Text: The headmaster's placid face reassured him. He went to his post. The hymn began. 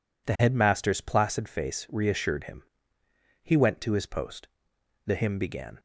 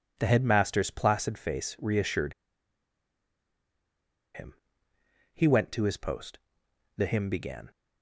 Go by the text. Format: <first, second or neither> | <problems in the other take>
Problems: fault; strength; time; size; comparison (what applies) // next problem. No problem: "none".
first | pauses between "reassured" and "him"; strong; at 2.3 s; 2.0 s long